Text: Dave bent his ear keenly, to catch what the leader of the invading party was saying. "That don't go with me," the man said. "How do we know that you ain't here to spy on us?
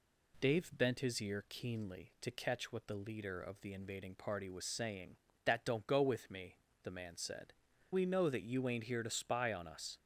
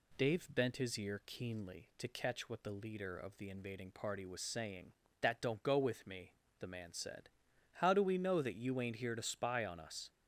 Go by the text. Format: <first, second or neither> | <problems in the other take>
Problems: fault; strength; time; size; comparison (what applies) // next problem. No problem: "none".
second | skips "How do"; at 7.7 s